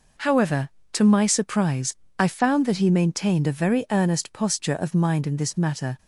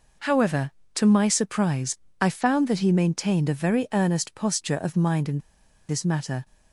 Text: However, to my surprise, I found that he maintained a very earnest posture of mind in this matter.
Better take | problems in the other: first | pauses between "in" and "this"; noticeable; at 5.3 s; 0.50 s long

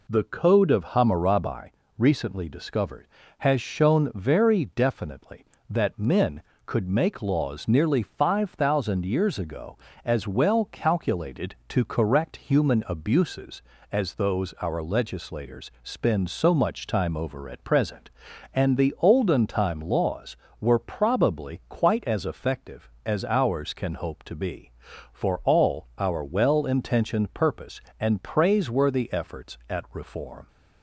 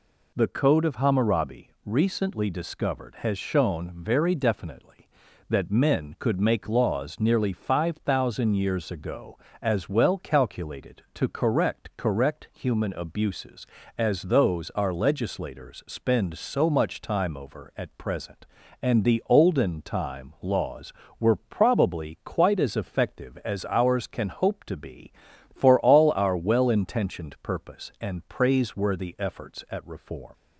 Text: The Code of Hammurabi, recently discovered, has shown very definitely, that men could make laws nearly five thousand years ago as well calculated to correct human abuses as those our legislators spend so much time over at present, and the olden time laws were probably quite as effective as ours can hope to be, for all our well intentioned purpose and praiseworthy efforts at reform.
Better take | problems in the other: first | says "correct" twice; at 11.9 s

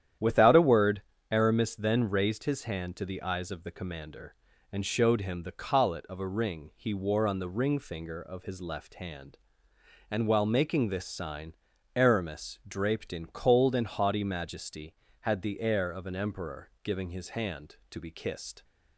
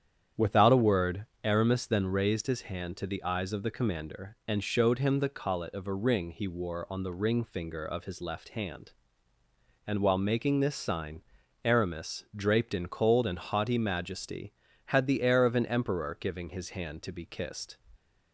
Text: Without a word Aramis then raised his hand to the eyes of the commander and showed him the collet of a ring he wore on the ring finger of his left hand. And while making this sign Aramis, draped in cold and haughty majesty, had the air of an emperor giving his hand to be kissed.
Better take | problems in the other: neither | starts louder than the rest; strong; the same in both // pauses between "word" and "Aramis"; slight; the same in both // pauses between "sign" and "Aramis"; the same in both

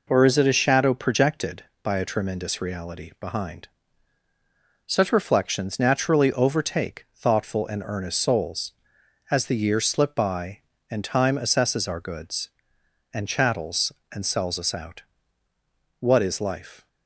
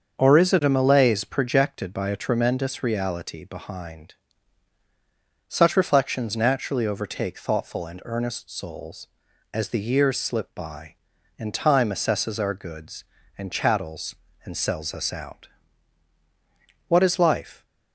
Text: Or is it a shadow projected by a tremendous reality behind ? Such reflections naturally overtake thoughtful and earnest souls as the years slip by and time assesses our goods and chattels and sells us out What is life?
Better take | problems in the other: first | starts louder than the rest; until 1.2 s; 6.5 dB // says "malaise" for "shadow"; at 0.6 s // pauses between "out" and "What"; strong; at 15.4 s; 1.4 s long; noticeable in the first

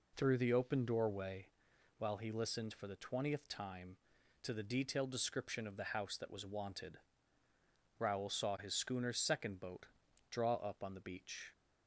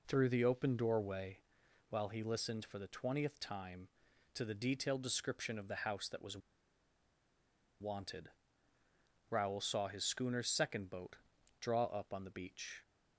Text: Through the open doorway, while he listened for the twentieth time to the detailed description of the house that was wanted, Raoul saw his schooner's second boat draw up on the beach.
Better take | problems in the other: first | pauses between "was" and "wanted"; strong; at 6.3 s; 1.4 s long // pauses between "boat" and "draw"; at 11.1 s; 0.42 s long; also in the first

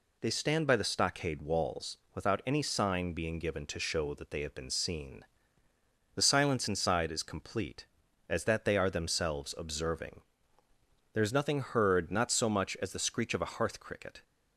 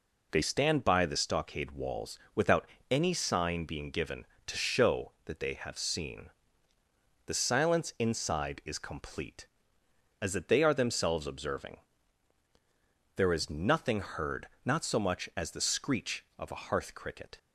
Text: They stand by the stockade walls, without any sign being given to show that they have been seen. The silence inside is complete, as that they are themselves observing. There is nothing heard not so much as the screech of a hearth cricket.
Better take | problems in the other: first | pauses between "without" and "any"; slight; at 2.6 s; 0.24 s long // skips "been"; at 5.7 s // pauses between "heard" and "not"; slight; at 14.4 s; 0.16 s long

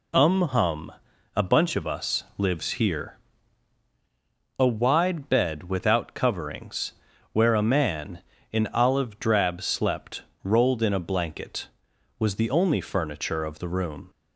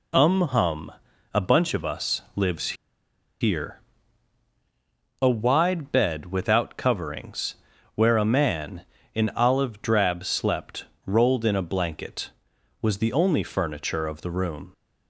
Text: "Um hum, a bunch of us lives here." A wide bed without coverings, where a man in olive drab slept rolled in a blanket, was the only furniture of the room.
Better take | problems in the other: first | pauses between "lives" and "here"; noticeable; at 2.7 s; 0.66 s long // pauses between "slept" and "rolled"; slight; at 10.8 s; 0.20 s long; slight in the first

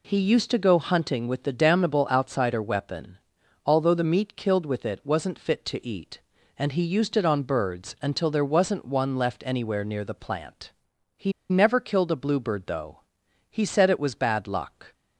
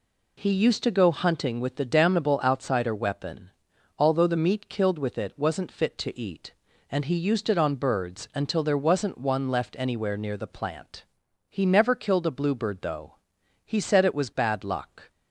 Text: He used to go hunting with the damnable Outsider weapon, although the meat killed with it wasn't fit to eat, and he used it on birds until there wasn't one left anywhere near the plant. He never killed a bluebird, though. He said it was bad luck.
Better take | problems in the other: second | pauses between "He" and "never"; slight; at 11.3 s; 0.19 s long

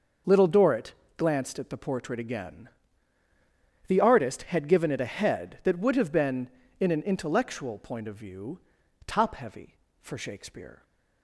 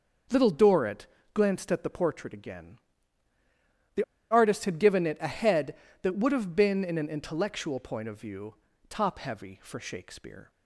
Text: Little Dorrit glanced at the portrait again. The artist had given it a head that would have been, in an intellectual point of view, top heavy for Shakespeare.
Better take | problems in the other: first | starts louder than the rest; until 1.6 s; 6.5 dB // pauses between "Dorrit" and "glanced"; slight; at 1.0 s; 0.28 s long; slight in the first // pauses between "The" and "artist"; slight; at 4.0 s; 0.27 s long

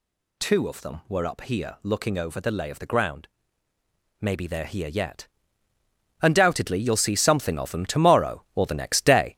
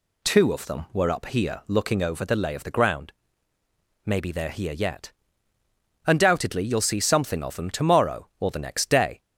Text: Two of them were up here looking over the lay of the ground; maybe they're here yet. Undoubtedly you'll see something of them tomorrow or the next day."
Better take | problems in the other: second | gets louder; throughout; 6 dB

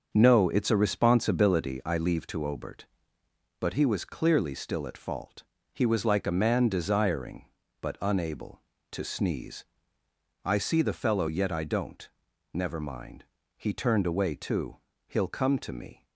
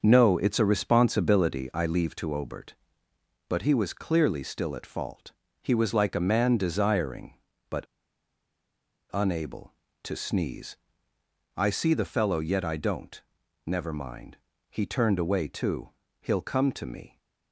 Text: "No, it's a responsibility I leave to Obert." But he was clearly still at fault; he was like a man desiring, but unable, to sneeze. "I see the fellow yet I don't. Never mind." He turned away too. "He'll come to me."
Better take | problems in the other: first | starts louder than the rest; until 1.0 s; 6.5 dB; also in the first // pauses between "but" and "unable"; strong; at 7.8 s; 1.2 s long

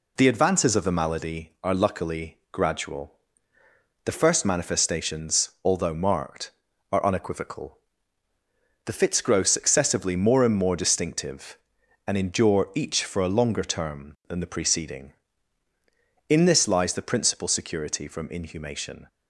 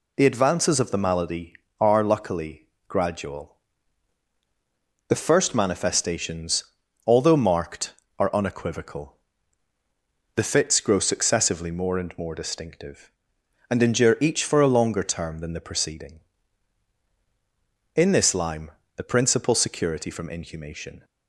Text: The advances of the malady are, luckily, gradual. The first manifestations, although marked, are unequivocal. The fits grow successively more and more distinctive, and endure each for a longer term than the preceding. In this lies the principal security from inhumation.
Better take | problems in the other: first | says "lime" for "lies"; at 18.3 s

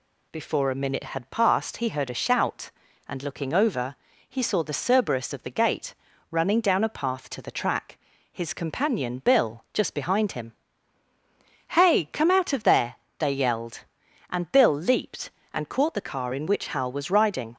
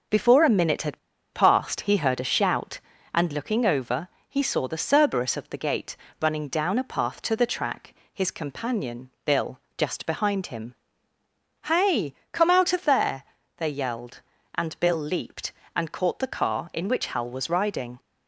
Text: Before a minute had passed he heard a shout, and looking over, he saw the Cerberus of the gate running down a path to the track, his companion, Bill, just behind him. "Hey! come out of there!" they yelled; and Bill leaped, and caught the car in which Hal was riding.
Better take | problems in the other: first | pauses between "had" and "passed"; slight; at 0.9 s; 0.34 s long // pauses between "gate" and "running"; slight; at 5.9 s; 0.26 s long; slight in the first

